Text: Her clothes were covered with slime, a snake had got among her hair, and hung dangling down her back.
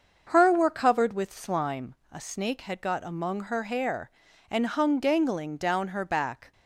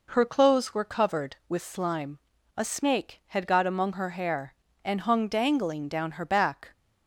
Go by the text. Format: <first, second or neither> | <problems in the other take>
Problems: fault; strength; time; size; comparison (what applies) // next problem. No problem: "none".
second | starts louder than the rest; until 1.3 s; 6.5 dB // skips "clothes"; at 0.5 s